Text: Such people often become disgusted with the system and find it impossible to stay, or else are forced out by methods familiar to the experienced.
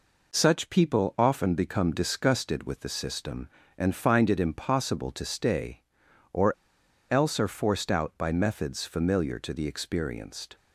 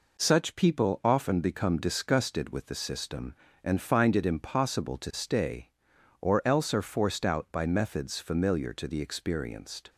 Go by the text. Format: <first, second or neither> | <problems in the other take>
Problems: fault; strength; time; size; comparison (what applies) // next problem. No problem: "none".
second | pauses between "or" and "else"; noticeable; at 6.5 s; 0.58 s long